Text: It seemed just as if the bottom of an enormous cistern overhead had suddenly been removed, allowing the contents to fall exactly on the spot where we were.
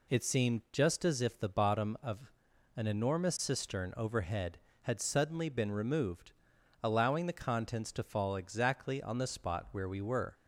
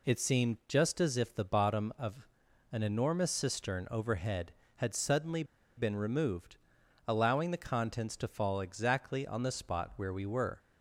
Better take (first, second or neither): first